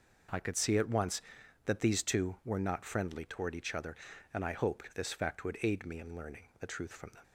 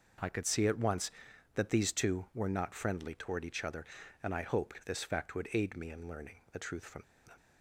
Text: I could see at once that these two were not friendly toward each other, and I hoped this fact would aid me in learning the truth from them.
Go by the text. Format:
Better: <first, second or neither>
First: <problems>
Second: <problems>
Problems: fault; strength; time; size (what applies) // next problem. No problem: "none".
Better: first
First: pauses between "learning" and "the"; slight; at 6.4 s; 0.18 s long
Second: pauses between "learning" and "the"; slight; at 6.3 s; 0.18 s long // pauses between "from" and "them"; slight; at 7.0 s; 0.22 s long